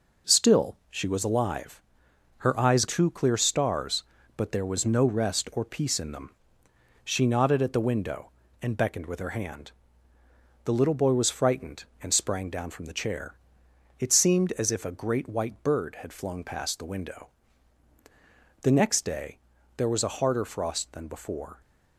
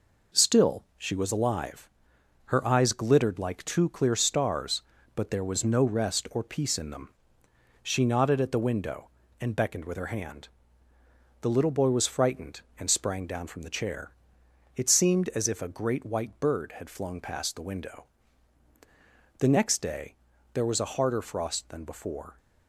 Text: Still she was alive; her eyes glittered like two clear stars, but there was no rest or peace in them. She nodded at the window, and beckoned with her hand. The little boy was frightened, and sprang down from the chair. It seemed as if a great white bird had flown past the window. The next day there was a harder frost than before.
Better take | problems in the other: second | skips "glittered like"; at 2.8 s // pauses between "day" and "there"; at 19.3 s; 0.38 s long; also in the second

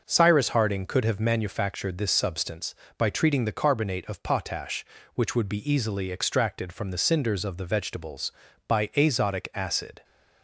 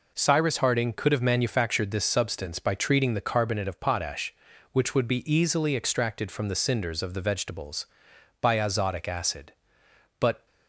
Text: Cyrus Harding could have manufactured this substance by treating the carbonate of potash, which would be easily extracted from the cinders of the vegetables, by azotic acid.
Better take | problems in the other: first | goes on to say "But"; slight; from 10.1 s on; 0.26 s long

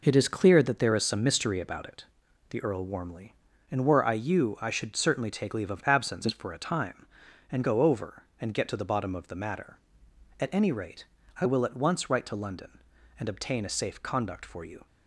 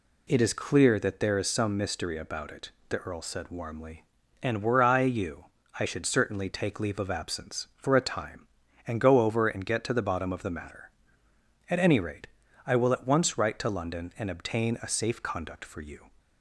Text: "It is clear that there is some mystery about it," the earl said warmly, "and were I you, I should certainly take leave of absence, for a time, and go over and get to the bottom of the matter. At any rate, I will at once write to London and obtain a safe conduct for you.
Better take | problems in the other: second | skips "said"; at 2.8 s

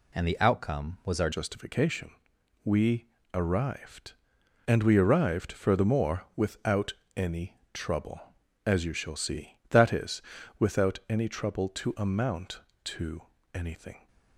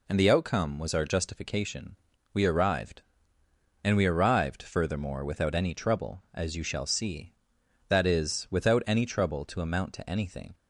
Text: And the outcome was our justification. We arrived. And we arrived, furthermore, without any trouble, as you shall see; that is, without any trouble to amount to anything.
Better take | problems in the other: second | changes voice at "justification"; from 1.3 s on; 12.7 s long // pauses between "We" and "arrived"; slight; at 3.0 s; 0.28 s long // pauses between "without" and "any"; slight; at 6.9 s; 0.22 s long // pauses between "to" and "anything"; slight; at 13.2 s; 0.32 s long

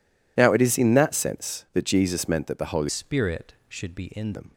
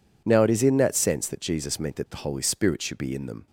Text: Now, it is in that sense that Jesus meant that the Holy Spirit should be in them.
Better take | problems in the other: second | changes voice from "Spirit" to "in"; from 2.8 to 4.3 s; 1.5 s long

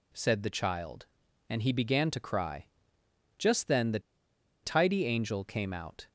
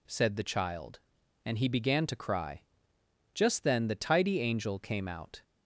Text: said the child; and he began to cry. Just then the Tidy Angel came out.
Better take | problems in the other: second | pauses between "the" and "Tidy"; noticeable; at 3.9 s; 0.64 s long

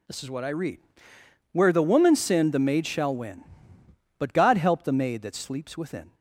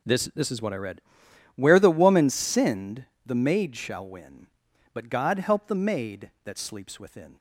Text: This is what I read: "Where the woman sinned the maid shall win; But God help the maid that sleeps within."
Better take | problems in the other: first | says "This" twice; at 0.3 s // pauses between "sinned" and "the"; slight; at 3.0 s; 0.20 s long

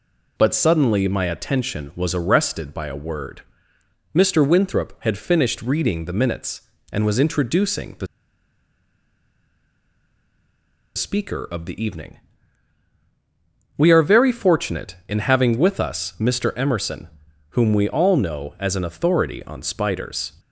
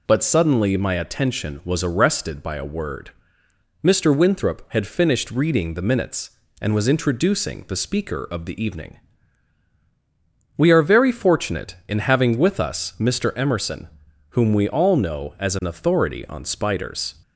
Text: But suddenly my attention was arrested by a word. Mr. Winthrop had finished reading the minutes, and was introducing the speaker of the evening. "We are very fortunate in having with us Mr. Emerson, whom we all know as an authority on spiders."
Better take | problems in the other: second | pauses between "the" and "speaker"; strong; at 8.0 s; 2.8 s long

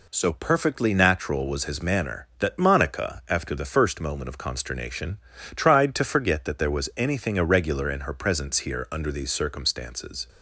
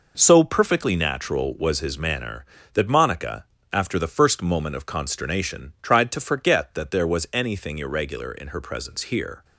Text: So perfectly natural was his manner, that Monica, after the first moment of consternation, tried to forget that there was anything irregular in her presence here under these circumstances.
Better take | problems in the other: first | stops before "under these circumstances"; at 9.4 s

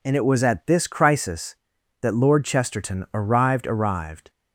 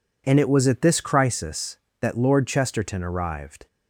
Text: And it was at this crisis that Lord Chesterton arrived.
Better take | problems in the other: second | says "arrived" twice; at 3.6 s

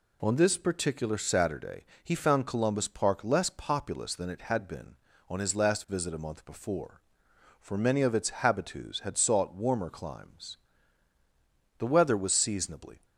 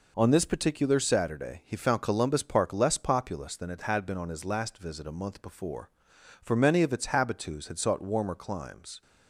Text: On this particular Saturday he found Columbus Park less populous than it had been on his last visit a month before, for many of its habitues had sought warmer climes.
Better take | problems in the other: second | pauses between "Saturday" and "he"; slight; at 1.8 s; 0.20 s long // goes on to say "The weather was seasonably"; noticeable; from 11.7 s on; 1.2 s long

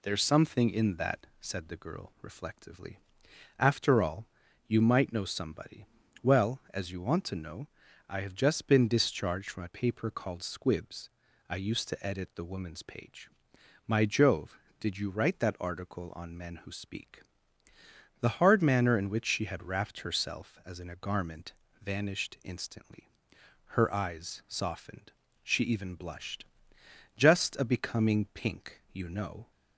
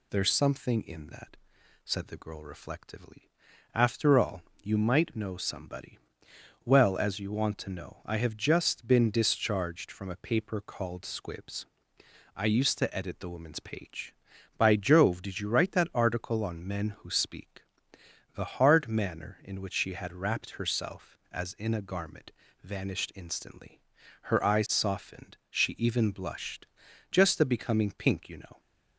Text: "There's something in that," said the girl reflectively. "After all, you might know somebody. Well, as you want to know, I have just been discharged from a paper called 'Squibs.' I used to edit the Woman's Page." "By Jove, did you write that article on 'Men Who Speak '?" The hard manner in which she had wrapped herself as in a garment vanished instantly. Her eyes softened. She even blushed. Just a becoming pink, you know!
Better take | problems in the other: second | says "My" for "By"; at 13.8 s // pauses between "garment" and "vanished"; slight; at 21.5 s; 0.30 s long; slight in the second

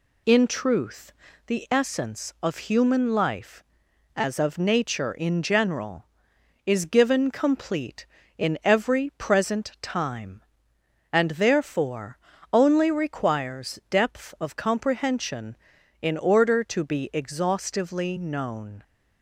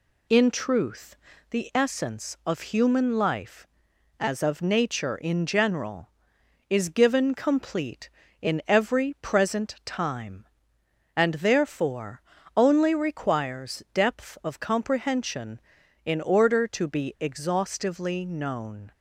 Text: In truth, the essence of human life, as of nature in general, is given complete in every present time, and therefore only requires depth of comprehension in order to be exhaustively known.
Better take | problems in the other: neither | pauses between "therefore" and "only"; slight; the same in both

